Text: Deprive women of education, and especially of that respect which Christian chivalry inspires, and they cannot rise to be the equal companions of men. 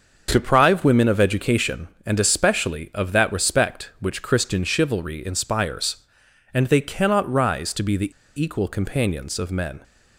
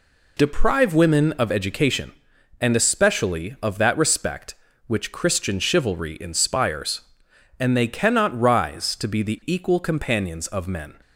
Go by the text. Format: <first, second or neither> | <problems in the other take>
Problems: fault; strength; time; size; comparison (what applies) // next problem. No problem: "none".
second | starts louder than the rest; until 1.3 s; 6.5 dB // pauses between "the" and "equal"; slight; at 8.1 s; 0.28 s long